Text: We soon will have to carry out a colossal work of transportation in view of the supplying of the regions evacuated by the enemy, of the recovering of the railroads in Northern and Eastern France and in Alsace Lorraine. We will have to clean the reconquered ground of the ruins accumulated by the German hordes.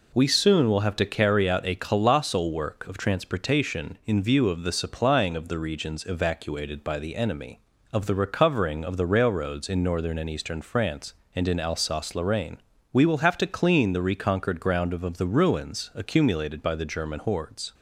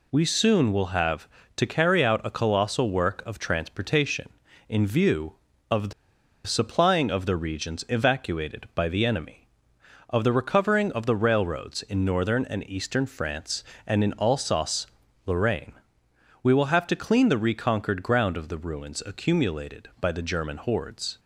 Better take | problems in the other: first | pauses between "the" and "supplying"; noticeable; at 5.9 s; 0.54 s long // pauses between "Alsace" and "Lorraine"; at 14.8 s; 0.40 s long

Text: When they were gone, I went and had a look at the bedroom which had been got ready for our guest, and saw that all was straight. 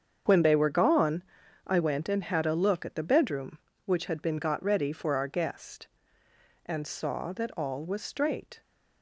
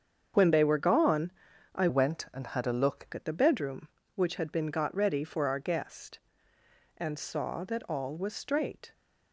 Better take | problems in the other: first | starts louder than the rest; strong; until 1.7 s; 7 dB; strong in the first // changes voice from "went" to "look"; from 1.8 to 3.0 s; 1.2 s long

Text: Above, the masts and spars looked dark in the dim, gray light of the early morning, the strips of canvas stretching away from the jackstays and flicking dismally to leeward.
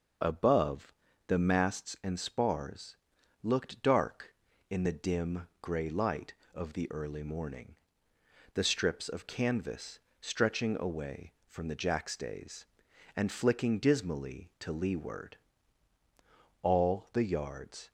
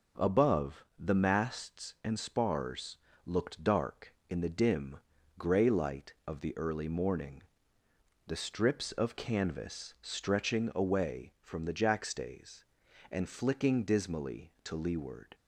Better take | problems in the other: second | pauses between "spars" and "looked"; noticeable; at 2.9 s; 0.46 s long; slight in the second // pauses between "canvas" and "stretching"; slight; at 9.9 s; 0.22 s long // goes on to say "All the yards"; noticeable; from 16.6 s on; 1.3 s long

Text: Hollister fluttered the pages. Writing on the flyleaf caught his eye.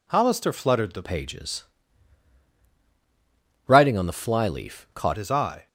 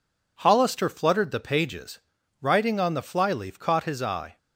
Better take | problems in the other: second | changes voice from "pages" to "caught"; from 1.0 to 5.1 s; 4.1 s long

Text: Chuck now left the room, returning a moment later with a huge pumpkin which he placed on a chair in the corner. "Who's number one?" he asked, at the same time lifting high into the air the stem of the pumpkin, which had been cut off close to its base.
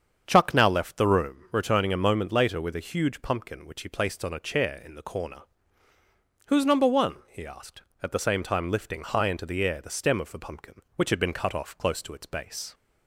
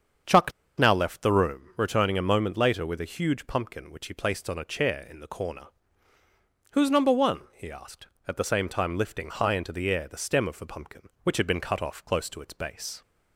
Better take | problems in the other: first | starts louder than the rest; until 1.5 s; 7 dB; strong in the first // pauses between "Chuck" and "now"; slight; at 0.5 s; 0.26 s long

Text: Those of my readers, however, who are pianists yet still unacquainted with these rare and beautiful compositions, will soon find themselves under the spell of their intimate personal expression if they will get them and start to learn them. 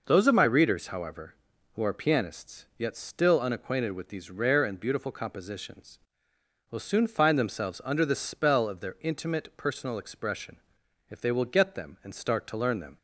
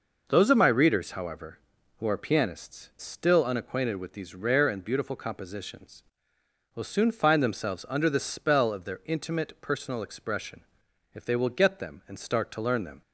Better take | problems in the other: first | skips "yet"; at 2.9 s // pauses between "expression" and "if"; noticeable; at 10.6 s; 0.52 s long; noticeable in the first

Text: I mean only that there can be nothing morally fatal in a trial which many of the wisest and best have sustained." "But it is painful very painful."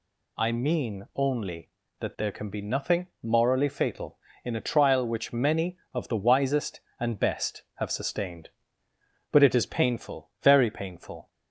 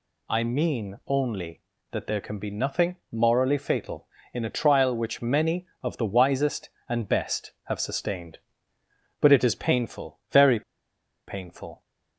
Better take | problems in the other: first | pauses between "nothing" and "morally"; slight; at 2.9 s; 0.16 s long; slight in the first // pauses between "very" and "painful"; noticeable; at 10.6 s; 0.66 s long

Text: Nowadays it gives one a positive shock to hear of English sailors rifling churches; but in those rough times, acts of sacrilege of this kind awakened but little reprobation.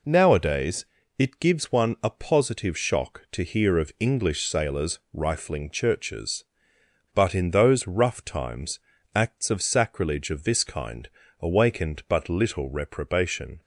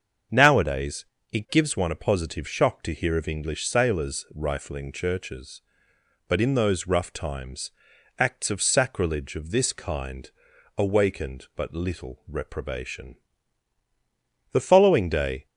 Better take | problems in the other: first | starts louder than the rest; until 1.6 s; 7 dB // pauses between "Nowadays" and "it"; slight; at 1.0 s; 0.26 s long; slight in the first // pauses between "kind" and "awakened"; noticeable; at 10.2 s; 0.48 s long; slight in the first // goes on to say "The following day"; noticeable; from 14.5 s on; 0.96 s long

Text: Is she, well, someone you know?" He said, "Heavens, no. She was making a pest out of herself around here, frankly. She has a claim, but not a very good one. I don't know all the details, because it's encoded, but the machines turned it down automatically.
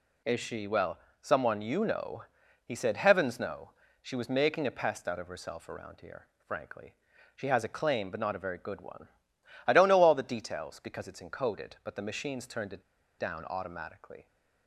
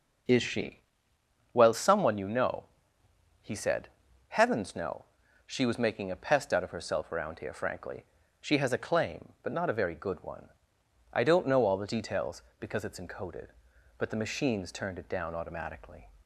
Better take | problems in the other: second | pauses between "it" and "down"; at 12.8 s; 0.37 s long

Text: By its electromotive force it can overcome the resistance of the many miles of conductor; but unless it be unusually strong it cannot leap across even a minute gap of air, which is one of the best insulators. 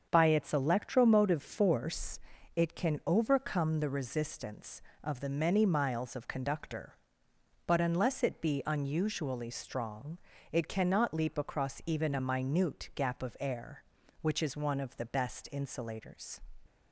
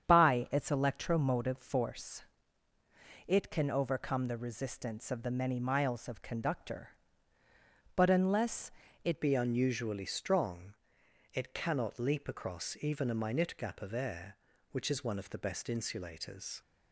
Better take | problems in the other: first | starts louder than the rest; strong; until 1.1 s; 8 dB; also in the first // pauses between "force" and "it"; at 2.2 s; 1.0 s long; also in the first // pauses between "unless" and "it"; slight; at 8.6 s; 0.36 s long // changes voice at "be"; from 9.2 s on; 7.4 s long // pauses between "strong" and "it"; noticeable; at 10.7 s; 0.58 s long; slight in the first

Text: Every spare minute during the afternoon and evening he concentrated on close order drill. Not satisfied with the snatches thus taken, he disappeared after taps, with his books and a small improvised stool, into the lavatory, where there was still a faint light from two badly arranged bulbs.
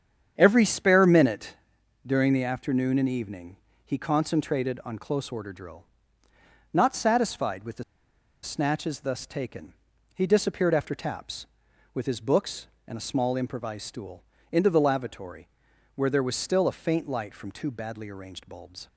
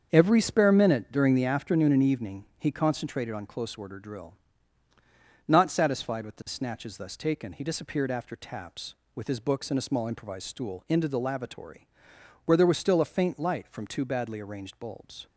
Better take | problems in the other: second | starts louder than the rest; strong; until 1.3 s; 8 dB; also in the second // pauses between "minute" and "during"; noticeable; at 1.5 s; 0.52 s long // pauses between "evening" and "he"; slight; at 3.5 s; 0.30 s long // pauses between "the" and "snatches"; noticeable; at 7.8 s; 0.61 s long

